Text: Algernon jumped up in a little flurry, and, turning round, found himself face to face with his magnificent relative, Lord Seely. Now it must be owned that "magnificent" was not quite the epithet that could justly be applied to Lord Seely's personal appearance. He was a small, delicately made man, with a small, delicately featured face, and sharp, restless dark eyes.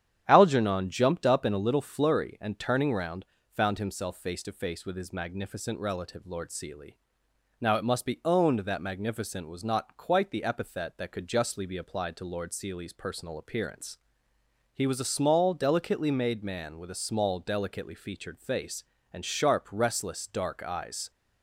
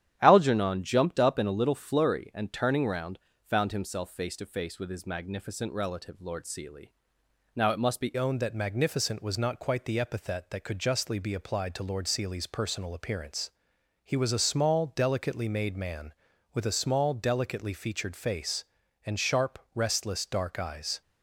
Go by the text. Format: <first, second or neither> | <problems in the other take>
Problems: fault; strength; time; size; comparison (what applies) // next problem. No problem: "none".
first | starts louder than the rest; strong; until 1.2 s; 10 dB; strong in the first // changes voice at "owned"; from 8.1 s on; 12.9 s long